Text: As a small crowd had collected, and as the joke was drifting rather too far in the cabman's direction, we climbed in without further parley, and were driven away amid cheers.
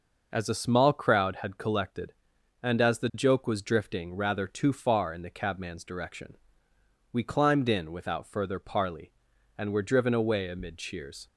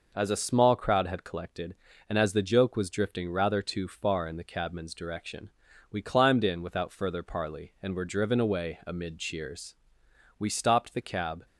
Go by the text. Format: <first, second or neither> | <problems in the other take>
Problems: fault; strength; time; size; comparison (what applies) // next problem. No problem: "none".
first | goes on to say "We stopped the cab"; noticeable; from 10.3 s on; 1.0 s long